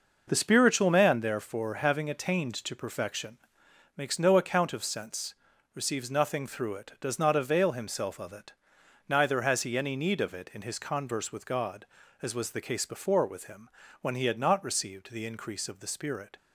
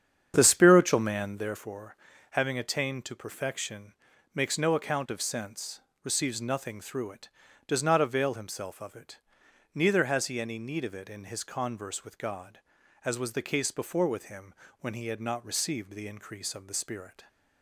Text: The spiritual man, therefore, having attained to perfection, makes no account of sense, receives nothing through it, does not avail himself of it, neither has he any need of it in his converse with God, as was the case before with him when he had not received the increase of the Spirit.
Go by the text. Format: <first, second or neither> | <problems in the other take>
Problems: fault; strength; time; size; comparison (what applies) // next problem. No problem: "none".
first | starts louder than the rest; strong; until 1.6 s; 8 dB // pauses between "him" and "when"; slight; at 14.5 s; 0.28 s long; slight in the first